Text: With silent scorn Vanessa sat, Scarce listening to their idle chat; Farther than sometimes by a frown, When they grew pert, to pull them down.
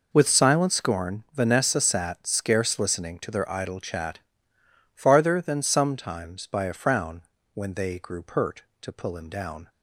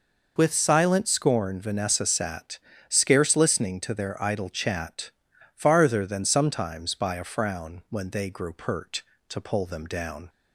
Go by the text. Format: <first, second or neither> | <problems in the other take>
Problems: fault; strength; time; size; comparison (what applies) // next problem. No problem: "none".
second | says "him" for "them"; at 9.1 s